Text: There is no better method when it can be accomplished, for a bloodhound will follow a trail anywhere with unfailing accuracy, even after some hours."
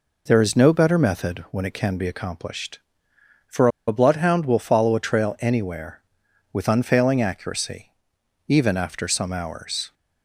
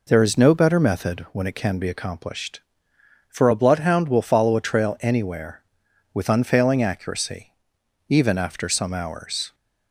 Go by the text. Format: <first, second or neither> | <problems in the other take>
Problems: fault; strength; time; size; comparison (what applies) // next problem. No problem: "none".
second | pauses between "for" and "a"; slight; at 3.6 s; 0.19 s long